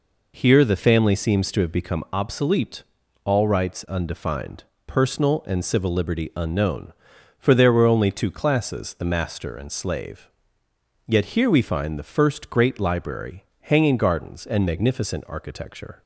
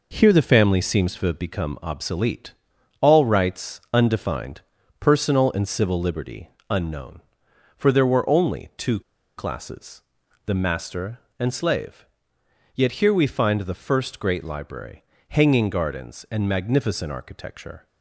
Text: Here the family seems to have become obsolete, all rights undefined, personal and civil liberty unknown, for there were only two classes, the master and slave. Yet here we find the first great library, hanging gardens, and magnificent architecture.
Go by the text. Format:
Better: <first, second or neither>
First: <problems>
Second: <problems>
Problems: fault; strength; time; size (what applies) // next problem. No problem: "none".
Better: first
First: none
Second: pauses between "liberty" and "unknown"; slight; at 6.4 s; 0.20 s long // pauses between "two" and "classes"; at 8.9 s; 0.37 s long